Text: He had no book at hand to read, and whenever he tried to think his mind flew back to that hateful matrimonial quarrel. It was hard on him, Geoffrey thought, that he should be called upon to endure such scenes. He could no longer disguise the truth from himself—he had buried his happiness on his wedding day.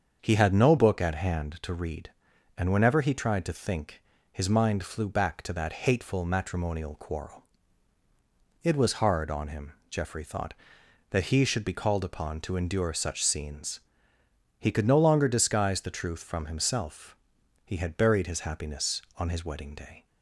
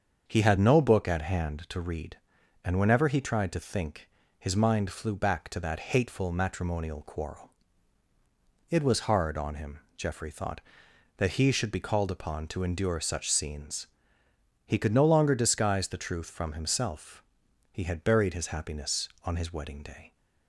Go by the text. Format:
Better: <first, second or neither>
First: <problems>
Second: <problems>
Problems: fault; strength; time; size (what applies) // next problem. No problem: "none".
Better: neither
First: starts louder than the rest; until 1.2 s; 7 dB // pauses between "think" and "his"; slight; at 4.0 s; 0.30 s long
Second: starts louder than the rest; until 1.2 s; 7 dB // pauses between "think" and "his"; slight; at 4.0 s; 0.30 s long